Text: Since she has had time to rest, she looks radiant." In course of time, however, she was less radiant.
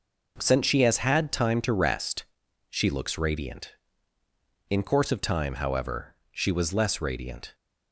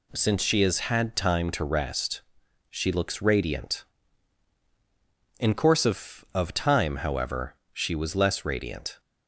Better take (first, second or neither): first